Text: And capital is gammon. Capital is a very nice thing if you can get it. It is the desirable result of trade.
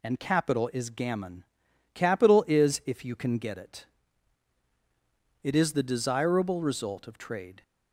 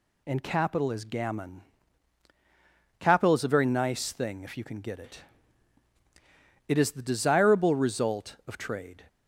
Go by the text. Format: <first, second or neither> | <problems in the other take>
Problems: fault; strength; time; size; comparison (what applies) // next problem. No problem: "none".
second | skips "a very nice thing"; at 2.8 s